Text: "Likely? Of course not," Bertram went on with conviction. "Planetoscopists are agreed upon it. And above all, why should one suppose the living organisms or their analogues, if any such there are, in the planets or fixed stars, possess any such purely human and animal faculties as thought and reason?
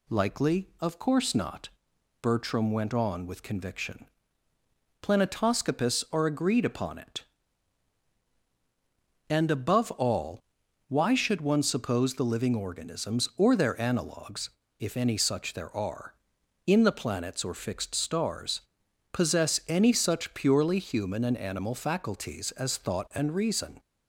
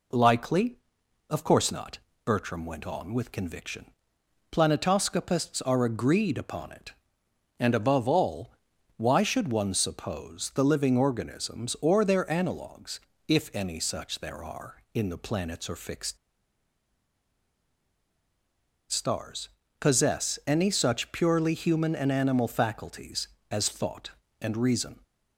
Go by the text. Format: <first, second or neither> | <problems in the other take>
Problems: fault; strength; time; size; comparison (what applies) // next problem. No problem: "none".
first | pauses between "fixed" and "stars"; strong; at 16.1 s; 2.7 s long